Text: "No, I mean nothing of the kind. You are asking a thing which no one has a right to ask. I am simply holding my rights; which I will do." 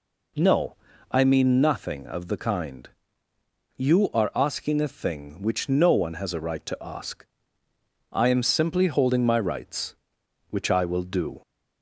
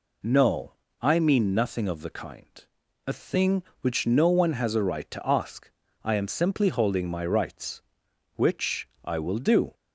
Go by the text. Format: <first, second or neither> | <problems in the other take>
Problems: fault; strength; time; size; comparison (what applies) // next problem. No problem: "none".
first | skips "You are asking"; at 2.8 s // pauses between "which" and "I"; slight; at 8.8 s; 0.16 s long